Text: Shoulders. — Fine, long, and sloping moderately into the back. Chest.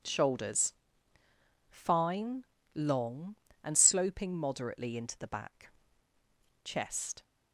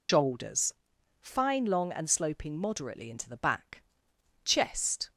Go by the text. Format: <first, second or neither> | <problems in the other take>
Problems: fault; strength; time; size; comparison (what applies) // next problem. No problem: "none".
first | loses the start of "Shoulders"; at 0.0 s; 145 ms